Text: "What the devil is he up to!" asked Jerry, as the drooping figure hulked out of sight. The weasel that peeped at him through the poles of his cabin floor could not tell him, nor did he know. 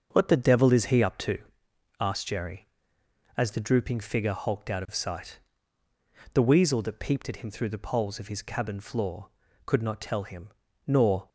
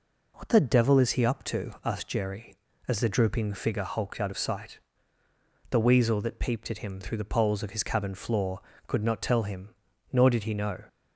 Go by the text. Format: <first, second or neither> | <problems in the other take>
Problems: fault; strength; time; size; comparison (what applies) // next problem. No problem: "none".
second | starts louder than the rest; until 1.1 s; 6.5 dB // stops before "did he know"; at 11.2 s